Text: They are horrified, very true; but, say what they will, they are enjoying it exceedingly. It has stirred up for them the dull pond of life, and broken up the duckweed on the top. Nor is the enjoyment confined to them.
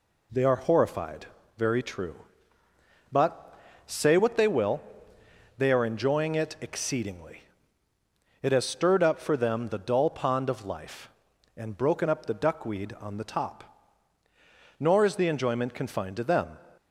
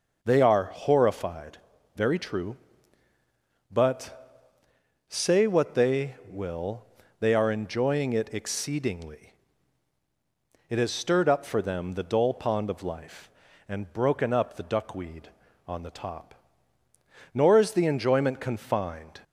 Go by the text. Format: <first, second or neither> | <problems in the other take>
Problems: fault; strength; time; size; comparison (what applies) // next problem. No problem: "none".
first | stops before "to them"; at 19.2 s